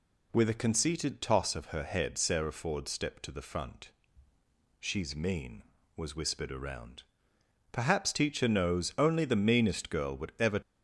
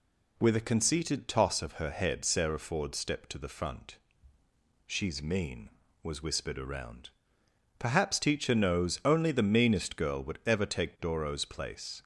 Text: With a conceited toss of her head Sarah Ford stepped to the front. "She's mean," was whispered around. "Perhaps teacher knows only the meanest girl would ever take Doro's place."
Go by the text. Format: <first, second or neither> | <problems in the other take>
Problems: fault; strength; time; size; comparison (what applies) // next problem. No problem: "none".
second | stops before "take Doro's place"; at 10.6 s